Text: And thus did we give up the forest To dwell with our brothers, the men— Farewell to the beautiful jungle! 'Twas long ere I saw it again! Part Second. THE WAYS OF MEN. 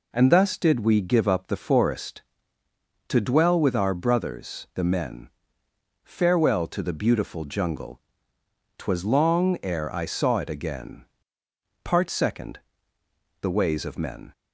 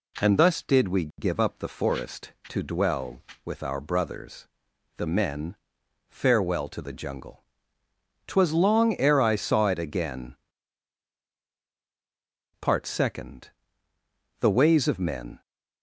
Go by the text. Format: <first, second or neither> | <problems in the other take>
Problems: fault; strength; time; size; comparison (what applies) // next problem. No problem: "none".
first | skips "beautiful"; at 6.9 s